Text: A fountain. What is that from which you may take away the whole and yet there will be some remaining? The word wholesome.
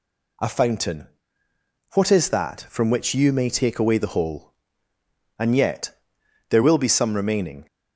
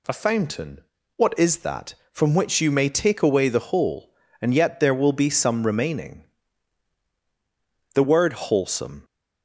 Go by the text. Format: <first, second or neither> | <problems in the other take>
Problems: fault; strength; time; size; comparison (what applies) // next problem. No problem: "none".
second | pauses between "yet" and "there"; noticeable; at 5.9 s; 0.58 s long // stops before "The word wholesome"; at 7.6 s